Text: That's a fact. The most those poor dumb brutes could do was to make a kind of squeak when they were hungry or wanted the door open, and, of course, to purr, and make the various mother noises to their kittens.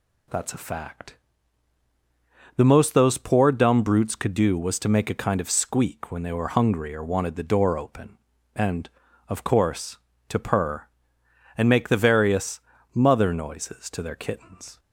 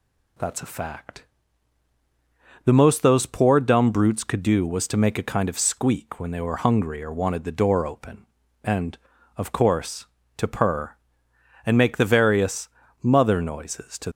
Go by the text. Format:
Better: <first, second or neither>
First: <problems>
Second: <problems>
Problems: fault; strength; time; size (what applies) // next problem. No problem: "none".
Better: first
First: pauses between "various" and "mother"; slight; at 12.5 s; 0.34 s long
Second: pauses between "various" and "mother"; slight; at 12.6 s; 0.34 s long // stops before "their kittens"; at 14.0 s